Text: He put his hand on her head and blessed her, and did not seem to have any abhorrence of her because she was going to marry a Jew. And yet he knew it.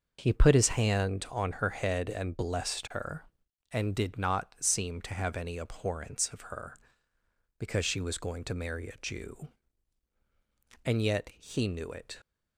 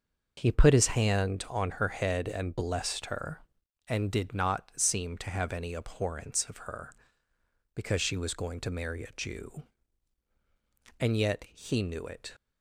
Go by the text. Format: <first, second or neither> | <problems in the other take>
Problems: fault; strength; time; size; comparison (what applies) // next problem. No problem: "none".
neither | none